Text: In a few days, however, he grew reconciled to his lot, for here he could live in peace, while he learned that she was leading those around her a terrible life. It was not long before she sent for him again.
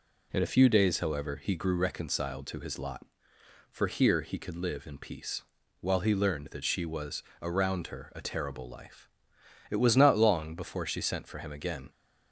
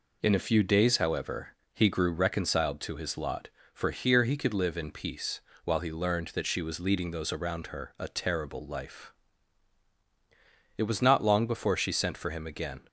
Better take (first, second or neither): second